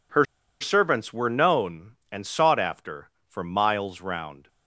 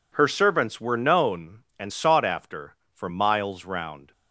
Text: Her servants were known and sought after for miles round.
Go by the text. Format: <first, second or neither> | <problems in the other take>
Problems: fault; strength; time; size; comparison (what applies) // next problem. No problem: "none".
second | pauses between "Her" and "servants"; at 0.2 s; 0.36 s long